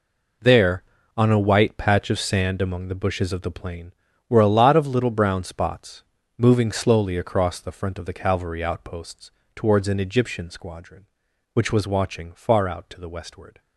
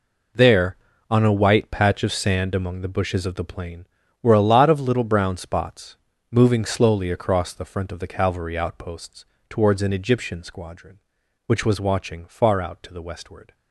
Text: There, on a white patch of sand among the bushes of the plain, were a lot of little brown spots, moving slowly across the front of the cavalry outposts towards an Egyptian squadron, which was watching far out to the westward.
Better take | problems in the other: neither | pauses between "outposts" and "towards"; slight; the same in both

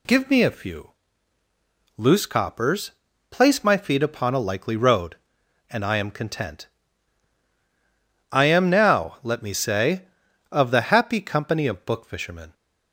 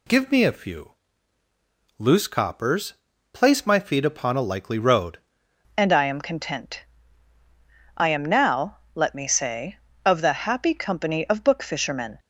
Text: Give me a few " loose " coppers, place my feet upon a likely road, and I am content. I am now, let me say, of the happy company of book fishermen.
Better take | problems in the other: first | changes voice at "and"; from 5.7 s on; 6.4 s long

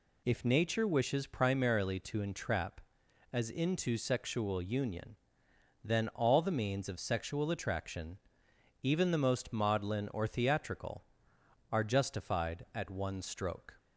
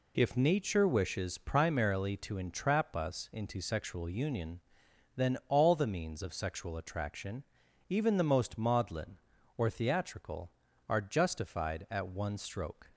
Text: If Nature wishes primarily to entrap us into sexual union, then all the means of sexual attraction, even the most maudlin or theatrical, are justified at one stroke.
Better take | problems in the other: second | says "as" for "us"; at 3.3 s

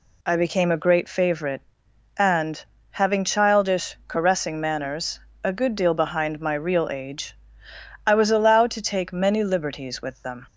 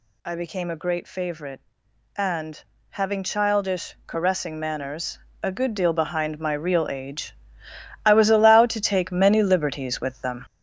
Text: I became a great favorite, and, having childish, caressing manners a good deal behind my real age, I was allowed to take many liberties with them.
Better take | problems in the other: first | gets louder; throughout; 6.5 dB // pauses between "manners" and "a"; slight; at 5.1 s; 0.24 s long; slight in the first

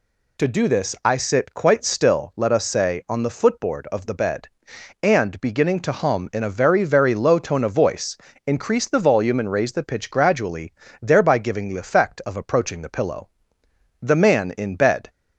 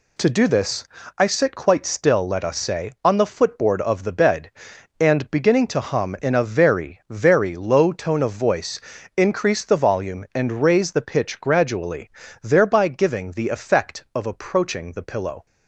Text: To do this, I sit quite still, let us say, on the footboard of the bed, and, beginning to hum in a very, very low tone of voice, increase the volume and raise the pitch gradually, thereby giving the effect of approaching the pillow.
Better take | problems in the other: second | goes on to say "The man in bed"; noticeable; from 14.0 s on; 1.0 s long

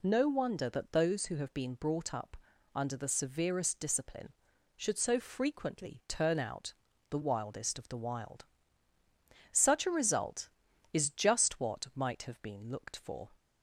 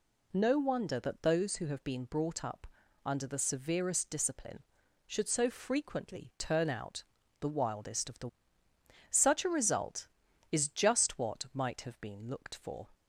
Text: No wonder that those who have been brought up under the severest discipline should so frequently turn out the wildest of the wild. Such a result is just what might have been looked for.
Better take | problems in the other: first | pauses between "up" and "under"; at 2.6 s; 0.38 s long; also in the first // pauses between "out" and "the"; at 7.0 s; 0.38 s long; also in the first // skips "wild"; at 8.6 s

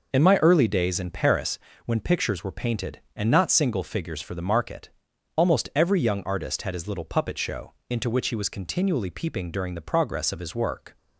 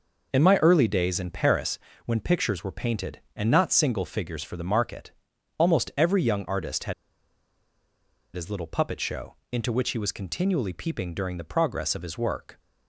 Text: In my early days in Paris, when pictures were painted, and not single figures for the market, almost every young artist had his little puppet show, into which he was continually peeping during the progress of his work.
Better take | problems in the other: first | pauses between "had" and "his"; strong; at 6.9 s; 1.4 s long

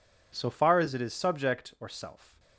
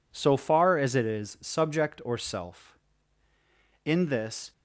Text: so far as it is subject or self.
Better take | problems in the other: first | goes on to say "In this"; noticeable; from 3.8 s on; 0.68 s long

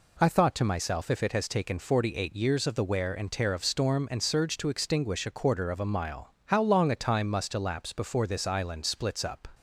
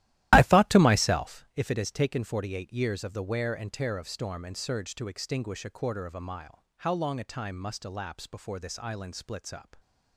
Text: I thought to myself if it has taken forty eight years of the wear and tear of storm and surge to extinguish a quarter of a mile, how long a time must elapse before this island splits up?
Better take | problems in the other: first | starts louder than the rest; strong; until 1.5 s; 14.5 dB

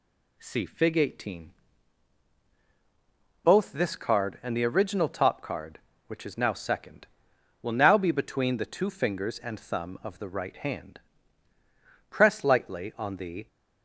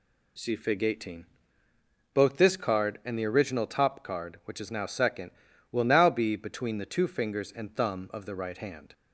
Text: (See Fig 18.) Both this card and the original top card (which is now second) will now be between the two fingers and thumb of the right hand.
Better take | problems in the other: second | goes on to say "Press lightly on the"; from 12.0 s on; 1.3 s long

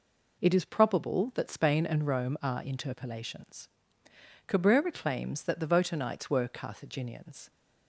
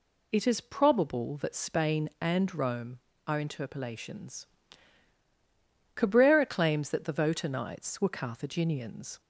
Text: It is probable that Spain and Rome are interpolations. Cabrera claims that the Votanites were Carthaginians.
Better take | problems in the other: neither | none

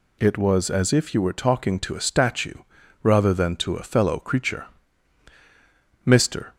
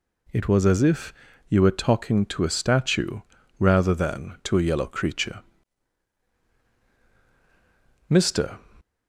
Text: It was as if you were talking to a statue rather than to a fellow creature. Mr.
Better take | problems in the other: first | pauses between "if" and "you"; slight; at 1.1 s; 0.34 s long // pauses between "statue" and "rather"; at 3.2 s; 0.38 s long; also in the first // says "yellow" for "fellow"; at 4.6 s

